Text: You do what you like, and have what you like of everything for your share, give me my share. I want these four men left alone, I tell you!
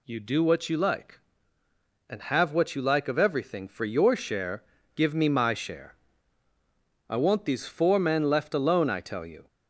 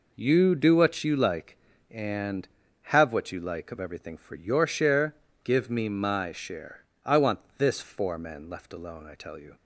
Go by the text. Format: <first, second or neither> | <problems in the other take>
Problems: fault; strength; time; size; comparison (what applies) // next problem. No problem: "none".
first | says "this" for "these"; at 7.5 s